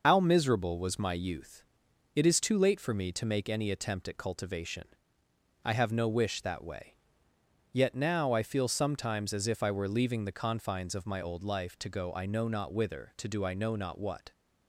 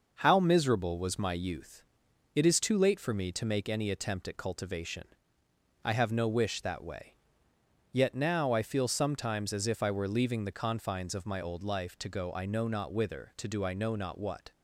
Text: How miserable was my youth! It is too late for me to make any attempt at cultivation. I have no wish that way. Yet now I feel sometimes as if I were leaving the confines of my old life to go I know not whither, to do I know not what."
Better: second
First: loses the start of "How"; at 0.0 s; 65 ms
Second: none

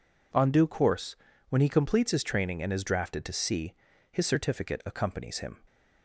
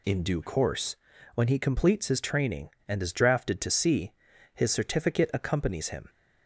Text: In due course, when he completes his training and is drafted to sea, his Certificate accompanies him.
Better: second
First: says "On" for "In"; at 0.3 s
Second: none

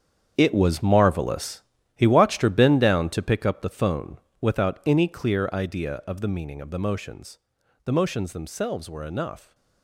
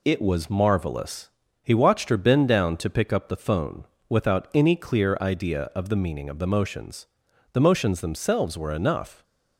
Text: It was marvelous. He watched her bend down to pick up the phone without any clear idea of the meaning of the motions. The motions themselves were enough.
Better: second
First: gets quieter; strong; throughout; 12 dB // pauses between "phone" and "without"; slight; at 4.1 s; 0.22 s long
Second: pauses between "phone" and "without"; slight; at 3.8 s; 0.24 s long

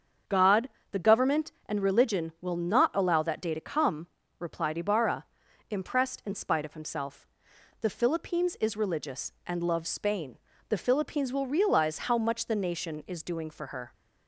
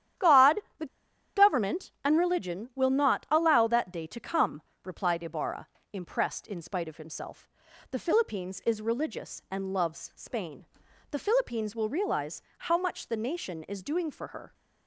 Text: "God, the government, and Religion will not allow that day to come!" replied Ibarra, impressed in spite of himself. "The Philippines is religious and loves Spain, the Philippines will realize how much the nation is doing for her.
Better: first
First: starts louder than the rest; until 1.4 s; 7 dB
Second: starts louder than the rest; strong; until 1.8 s; 10.5 dB // pauses between "the" and "government"; noticeable; at 0.8 s; 0.50 s long // pauses between "realize" and "how"; slight; at 12.4 s; 0.18 s long

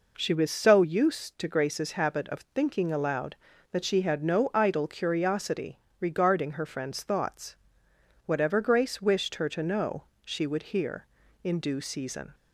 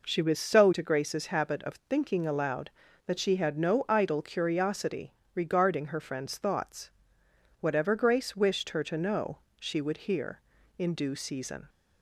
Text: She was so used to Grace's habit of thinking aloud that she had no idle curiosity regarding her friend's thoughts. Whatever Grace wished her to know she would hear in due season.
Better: first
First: pauses between "curiosity" and "regarding"; slight; at 5.8 s; 0.20 s long // pauses between "know" and "she"; slight; at 10.0 s; 0.20 s long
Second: skips "used"; at 0.7 s // pauses between "curiosity" and "regarding"; slight; at 5.1 s; 0.20 s long // pauses between "know" and "she"; slight; at 9.3 s; 0.20 s long

